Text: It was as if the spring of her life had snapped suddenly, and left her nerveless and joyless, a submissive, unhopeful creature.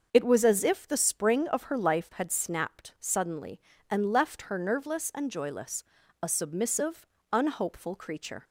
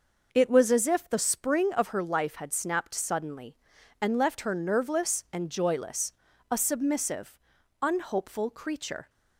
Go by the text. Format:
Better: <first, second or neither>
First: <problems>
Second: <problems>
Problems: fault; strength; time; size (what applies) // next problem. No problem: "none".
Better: neither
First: starts louder than the rest; until 1.1 s; 6.5 dB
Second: starts louder than the rest; noticeable; until 1.3 s; 6 dB